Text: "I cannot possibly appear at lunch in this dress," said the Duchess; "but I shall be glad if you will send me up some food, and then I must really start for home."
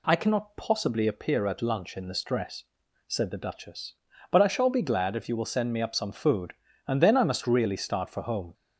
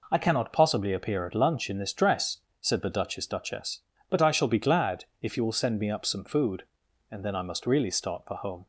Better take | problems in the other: first | says "Duchess" twice; at 3.2 s // pauses between "glad" and "if"; slight; at 5.0 s; 0.16 s long

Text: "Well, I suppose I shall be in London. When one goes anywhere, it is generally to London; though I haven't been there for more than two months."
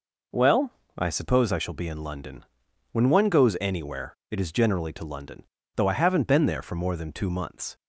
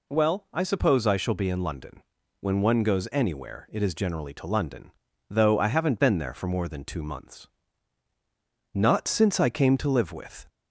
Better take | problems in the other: first | goes on to say "Not since I came to live with"; strong; from 8.7 s on; 1.7 s long

